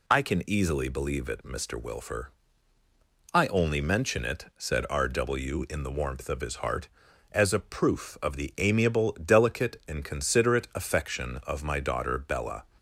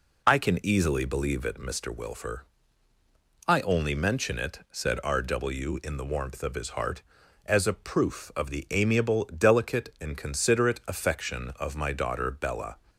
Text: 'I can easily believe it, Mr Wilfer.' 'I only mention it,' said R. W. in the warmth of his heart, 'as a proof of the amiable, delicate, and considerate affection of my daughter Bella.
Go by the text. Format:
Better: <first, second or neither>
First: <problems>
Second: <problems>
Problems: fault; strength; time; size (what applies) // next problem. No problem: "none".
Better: first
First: none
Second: starts louder than the rest; until 2.0 s; 3.5 dB